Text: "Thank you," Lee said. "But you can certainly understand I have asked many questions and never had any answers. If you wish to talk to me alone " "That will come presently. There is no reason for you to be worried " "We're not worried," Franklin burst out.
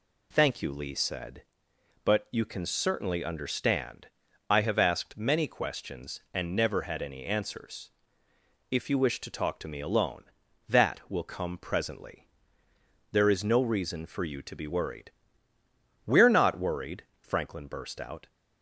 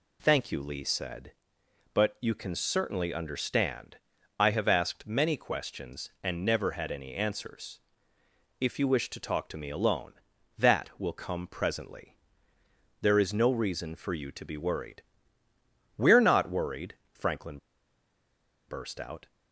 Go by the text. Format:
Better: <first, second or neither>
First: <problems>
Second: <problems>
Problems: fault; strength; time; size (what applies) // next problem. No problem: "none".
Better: first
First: pauses between "understand" and "I"; at 4.0 s; 0.42 s long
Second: pauses between "understand" and "I"; at 3.9 s; 0.42 s long // pauses between "Franklin" and "burst"; at 17.5 s; 1.1 s long